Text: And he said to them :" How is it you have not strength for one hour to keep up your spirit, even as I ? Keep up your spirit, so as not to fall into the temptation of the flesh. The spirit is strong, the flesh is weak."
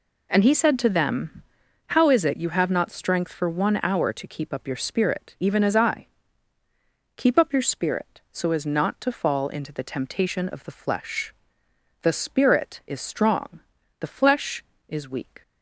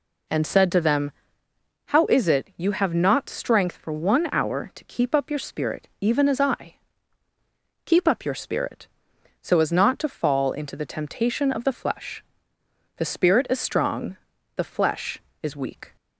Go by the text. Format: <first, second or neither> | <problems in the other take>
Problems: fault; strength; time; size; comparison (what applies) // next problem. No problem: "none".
first | skips "he"; at 0.4 s